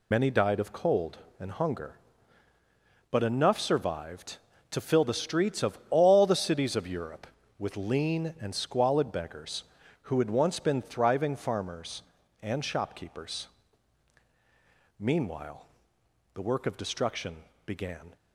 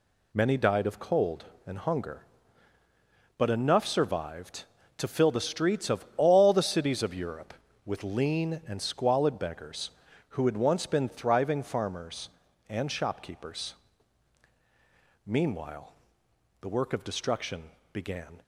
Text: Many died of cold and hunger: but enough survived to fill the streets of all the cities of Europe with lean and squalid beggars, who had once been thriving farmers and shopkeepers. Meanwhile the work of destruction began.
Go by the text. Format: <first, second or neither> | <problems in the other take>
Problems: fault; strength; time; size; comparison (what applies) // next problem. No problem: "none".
second | loses the start of "Many"; at 0.1 s; 35 ms // pauses between "Meanwhile" and "the"; noticeable; at 15.6 s; 0.70 s long; noticeable in the second // pauses between "destruction" and "began"; slight; at 17.3 s; 0.30 s long; slight in the second